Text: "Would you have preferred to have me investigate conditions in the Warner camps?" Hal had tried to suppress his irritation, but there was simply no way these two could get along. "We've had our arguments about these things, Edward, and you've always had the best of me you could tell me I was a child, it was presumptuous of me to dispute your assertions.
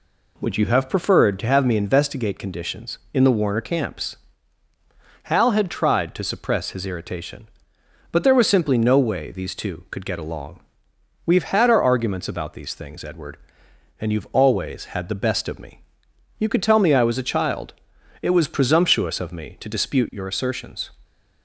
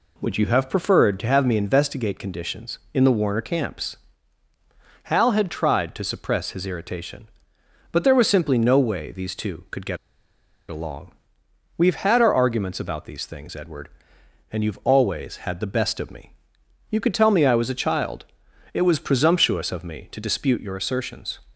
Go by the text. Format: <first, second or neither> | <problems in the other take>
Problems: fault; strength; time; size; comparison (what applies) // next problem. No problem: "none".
first | pauses between "get" and "along"; noticeable; at 9.9 s; 0.72 s long // pauses between "me" and "you"; noticeable; at 16.3 s; 0.58 s long; noticeable in the first